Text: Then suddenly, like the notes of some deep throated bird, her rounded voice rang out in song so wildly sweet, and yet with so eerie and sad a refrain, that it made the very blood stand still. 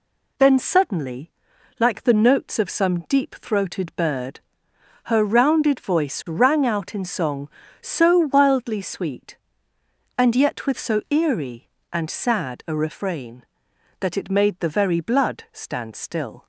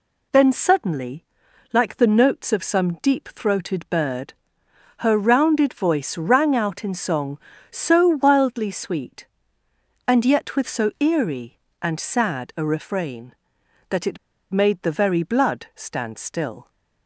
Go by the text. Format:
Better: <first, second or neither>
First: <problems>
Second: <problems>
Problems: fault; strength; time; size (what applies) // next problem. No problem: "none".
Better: first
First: none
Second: pauses between "it" and "made"; slight; at 14.1 s; 0.34 s long